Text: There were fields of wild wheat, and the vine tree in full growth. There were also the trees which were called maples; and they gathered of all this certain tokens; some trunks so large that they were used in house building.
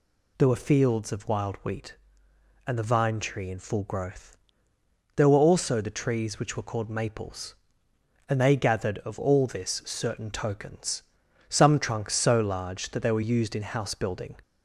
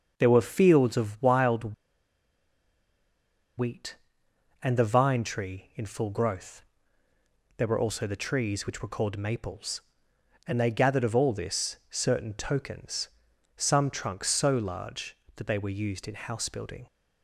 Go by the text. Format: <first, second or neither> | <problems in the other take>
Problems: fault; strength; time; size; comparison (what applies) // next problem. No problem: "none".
first | pauses between "wild" and "wheat"; strong; at 1.7 s; 1.8 s long // pauses between "this" and "certain"; slight; at 11.7 s; 0.16 s long